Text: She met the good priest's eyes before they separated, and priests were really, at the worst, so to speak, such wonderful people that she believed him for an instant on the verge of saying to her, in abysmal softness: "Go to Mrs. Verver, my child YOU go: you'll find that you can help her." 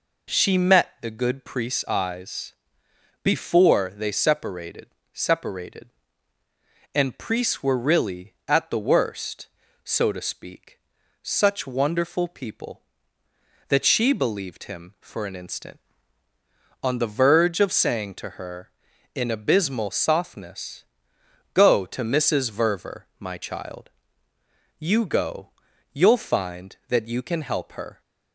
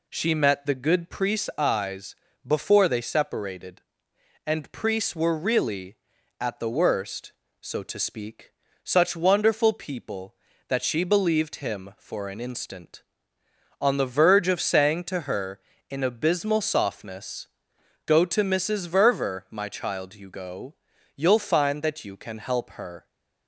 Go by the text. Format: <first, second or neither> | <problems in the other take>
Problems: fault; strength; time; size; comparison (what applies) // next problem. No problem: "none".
second | pauses between "eyes" and "before"; noticeable; at 2.5 s; 0.72 s long; slight in the second // says "separated" twice; at 5.1 s // pauses between "child" and "YOU"; noticeable; at 23.9 s; 0.86 s long